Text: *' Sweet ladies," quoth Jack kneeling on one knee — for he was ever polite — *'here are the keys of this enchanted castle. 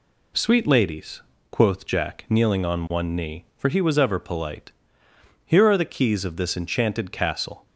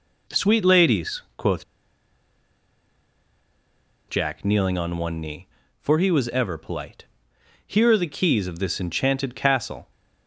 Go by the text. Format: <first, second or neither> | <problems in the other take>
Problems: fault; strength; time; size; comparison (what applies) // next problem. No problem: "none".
first | pauses between "quoth" and "Jack"; strong; at 1.6 s; 2.4 s long